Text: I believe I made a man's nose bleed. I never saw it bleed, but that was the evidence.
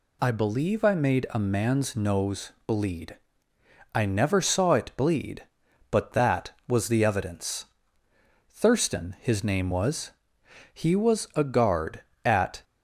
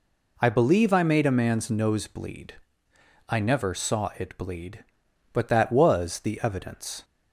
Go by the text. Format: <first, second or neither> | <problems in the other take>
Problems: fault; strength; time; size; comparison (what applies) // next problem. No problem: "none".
second | goes on to say "Thurston his name was He was a guard at"; strong; from 8.5 s on; 4.1 s long